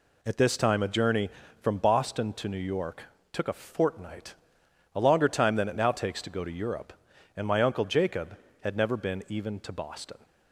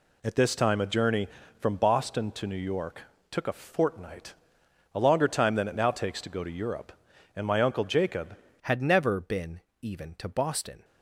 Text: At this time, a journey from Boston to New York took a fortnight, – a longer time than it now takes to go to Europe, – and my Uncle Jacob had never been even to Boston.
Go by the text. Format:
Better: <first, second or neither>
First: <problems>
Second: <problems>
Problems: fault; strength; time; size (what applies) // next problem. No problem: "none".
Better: first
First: pauses between "York" and "took"; slight; at 3.0 s; 0.28 s long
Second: pauses between "York" and "took"; slight; at 3.0 s; 0.28 s long // changes voice at "had"; from 8.6 s on; 2.2 s long // pauses between "been" and "even"; slight; at 9.6 s; 0.22 s long